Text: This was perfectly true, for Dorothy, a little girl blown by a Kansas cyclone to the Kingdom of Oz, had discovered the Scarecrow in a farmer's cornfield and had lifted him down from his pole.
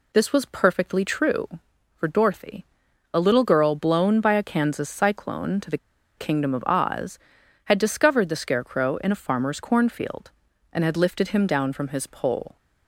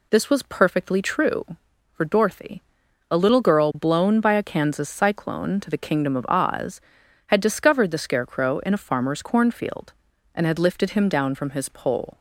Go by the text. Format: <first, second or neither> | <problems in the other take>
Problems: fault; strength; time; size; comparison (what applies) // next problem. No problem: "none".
second | pauses between "the" and "Kingdom"; at 5.7 s; 0.40 s long